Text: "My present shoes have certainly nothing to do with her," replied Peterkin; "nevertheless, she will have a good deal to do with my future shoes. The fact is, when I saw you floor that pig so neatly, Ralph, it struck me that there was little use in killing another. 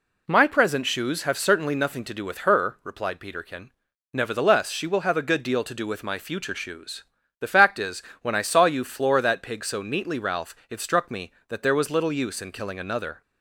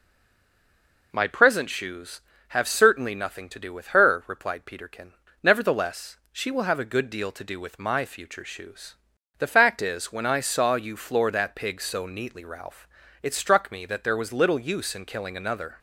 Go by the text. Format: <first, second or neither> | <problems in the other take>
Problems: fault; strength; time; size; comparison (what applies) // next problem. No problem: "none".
first | stays silent before the first word; until 1.1 s; 1.1 s long